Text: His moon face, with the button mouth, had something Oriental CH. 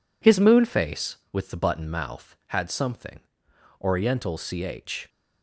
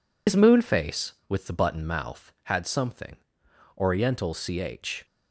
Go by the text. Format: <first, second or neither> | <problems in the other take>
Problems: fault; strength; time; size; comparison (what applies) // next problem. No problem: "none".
first | loses the start of "His"; at 0.2 s; 80 ms // pauses between "something" and "Oriental"; noticeable; at 3.1 s; 0.64 s long; noticeable in the first